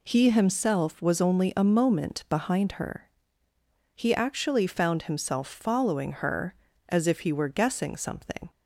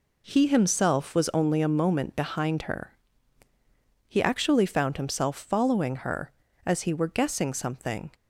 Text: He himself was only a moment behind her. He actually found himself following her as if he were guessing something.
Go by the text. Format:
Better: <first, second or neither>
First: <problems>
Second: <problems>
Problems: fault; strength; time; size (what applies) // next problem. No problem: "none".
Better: first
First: none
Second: skips "if"; at 6.8 s